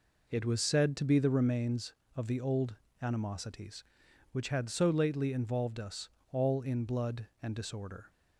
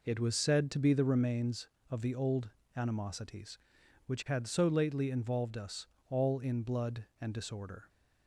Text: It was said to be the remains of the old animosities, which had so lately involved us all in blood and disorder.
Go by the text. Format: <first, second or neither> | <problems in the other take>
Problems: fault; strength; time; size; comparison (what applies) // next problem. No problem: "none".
neither | pauses between "old" and "animosities"; slight; the same in both // pauses between "us" and "all"; slight; the same in both